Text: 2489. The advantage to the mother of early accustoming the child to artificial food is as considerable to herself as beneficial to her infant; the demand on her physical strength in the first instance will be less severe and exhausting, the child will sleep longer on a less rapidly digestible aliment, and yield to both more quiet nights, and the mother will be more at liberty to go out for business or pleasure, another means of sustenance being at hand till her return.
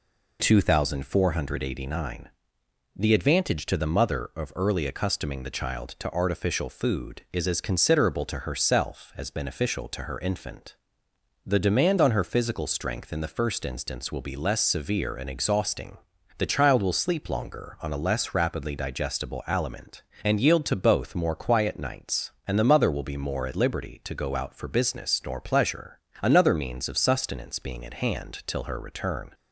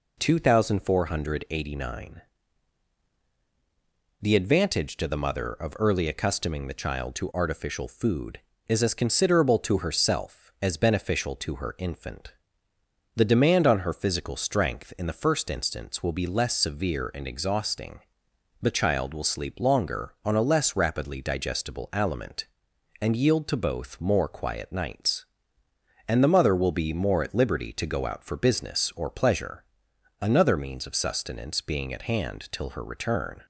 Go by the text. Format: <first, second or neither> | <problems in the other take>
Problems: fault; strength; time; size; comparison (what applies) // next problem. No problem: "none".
second | says "nor" for "or"; at 25.2 s